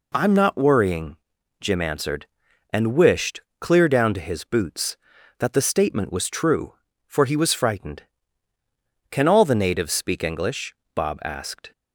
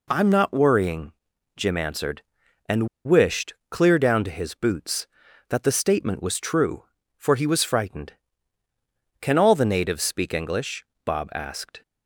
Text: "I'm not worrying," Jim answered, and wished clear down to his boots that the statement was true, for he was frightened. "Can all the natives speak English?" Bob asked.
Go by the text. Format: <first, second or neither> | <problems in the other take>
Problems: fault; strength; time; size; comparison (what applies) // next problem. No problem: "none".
first | pauses between "and" and "wished"; slight; at 2.8 s; 0.17 s long // pauses between "wished" and "clear"; slight; at 3.5 s; 0.16 s long; slight in the first